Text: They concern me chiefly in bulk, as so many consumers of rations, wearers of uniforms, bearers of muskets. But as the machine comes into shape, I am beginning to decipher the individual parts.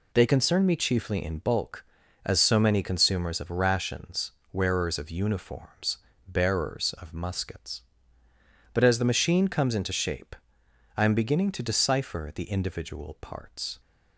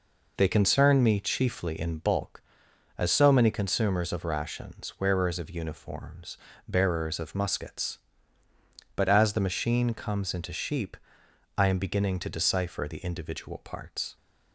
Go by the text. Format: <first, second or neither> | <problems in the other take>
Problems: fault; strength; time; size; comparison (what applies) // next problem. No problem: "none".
first | says "sheep" for "shape"; at 10.5 s